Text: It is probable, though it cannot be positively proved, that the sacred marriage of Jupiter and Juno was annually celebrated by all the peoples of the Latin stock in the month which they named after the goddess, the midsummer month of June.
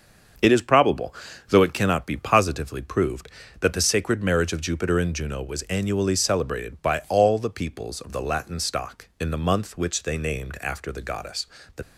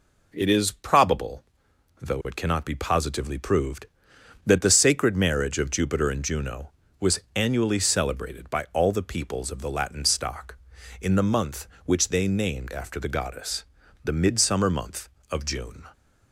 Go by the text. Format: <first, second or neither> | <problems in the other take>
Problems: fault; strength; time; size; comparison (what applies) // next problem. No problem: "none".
second | starts louder than the rest; until 1.7 s; 7 dB // stops before "midsummer month of June"; at 11.8 s